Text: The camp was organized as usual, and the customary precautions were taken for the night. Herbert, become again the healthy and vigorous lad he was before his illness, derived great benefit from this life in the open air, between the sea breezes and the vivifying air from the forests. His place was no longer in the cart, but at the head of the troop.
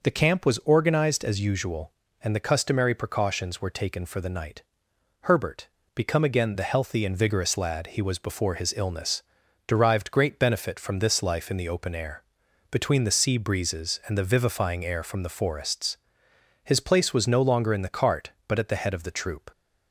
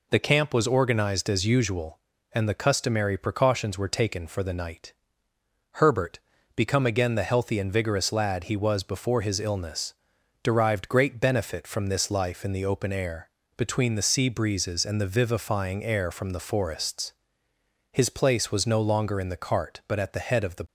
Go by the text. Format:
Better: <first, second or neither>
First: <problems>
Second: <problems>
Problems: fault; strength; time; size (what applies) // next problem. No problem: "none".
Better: first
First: none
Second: stops before "troop"; at 20.6 s